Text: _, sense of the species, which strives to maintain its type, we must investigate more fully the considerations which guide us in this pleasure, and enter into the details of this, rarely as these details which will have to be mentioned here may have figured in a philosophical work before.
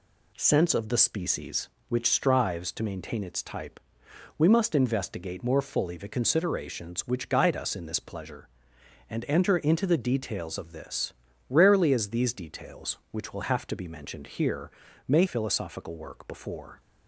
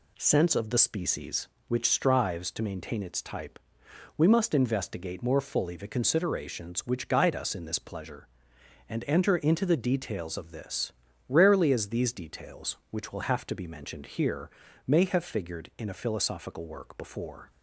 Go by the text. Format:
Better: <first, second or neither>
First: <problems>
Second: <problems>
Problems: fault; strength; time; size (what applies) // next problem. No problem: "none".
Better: second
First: pauses between "here" and "may"; slight; at 14.7 s; 0.34 s long // skips "have figured in a"; at 15.2 s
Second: pauses between "here" and "may"; slight; at 14.5 s; 0.34 s long